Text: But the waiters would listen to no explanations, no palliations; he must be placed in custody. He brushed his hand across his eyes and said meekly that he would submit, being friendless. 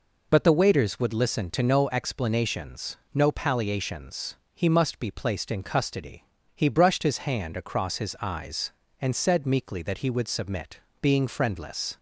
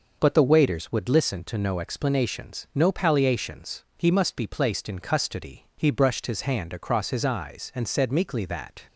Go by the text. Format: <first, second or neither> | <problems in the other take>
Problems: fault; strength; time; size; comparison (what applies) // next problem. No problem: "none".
first | stops before "he would submit being friendless"; at 8.8 s